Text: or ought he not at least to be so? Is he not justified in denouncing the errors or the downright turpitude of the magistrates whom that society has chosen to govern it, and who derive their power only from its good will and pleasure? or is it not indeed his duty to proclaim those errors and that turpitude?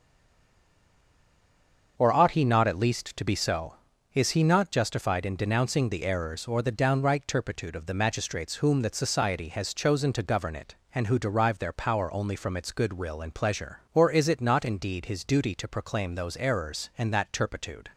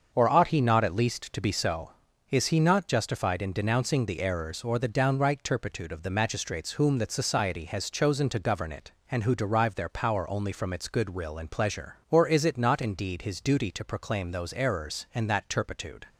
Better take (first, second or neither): second